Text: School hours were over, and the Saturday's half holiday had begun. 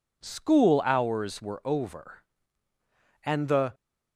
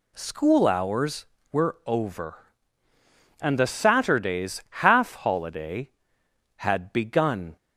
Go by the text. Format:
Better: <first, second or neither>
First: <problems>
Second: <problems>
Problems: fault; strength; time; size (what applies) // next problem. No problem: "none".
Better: second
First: stops before "Saturday's half holiday had begun"; at 3.7 s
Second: none